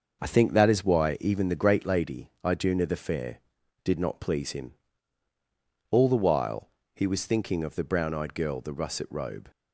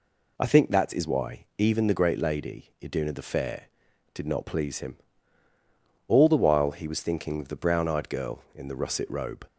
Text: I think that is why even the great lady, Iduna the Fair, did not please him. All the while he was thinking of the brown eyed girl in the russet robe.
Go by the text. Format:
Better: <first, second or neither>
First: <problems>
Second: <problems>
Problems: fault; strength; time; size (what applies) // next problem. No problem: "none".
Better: second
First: starts louder than the rest; noticeable; until 1.2 s; 6 dB // pauses between "while" and "he"; slight; at 6.6 s; 0.26 s long // skips "in"; at 8.5 s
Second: none